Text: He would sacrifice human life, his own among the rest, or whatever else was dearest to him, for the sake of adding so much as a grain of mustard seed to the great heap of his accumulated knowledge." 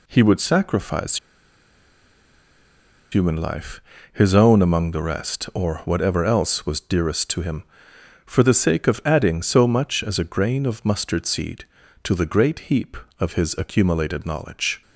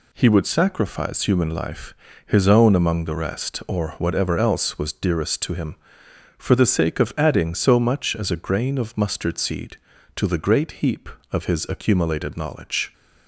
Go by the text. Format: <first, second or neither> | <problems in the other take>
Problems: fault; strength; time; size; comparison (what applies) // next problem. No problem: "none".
second | pauses between "sacrifice" and "human"; strong; at 1.1 s; 1.9 s long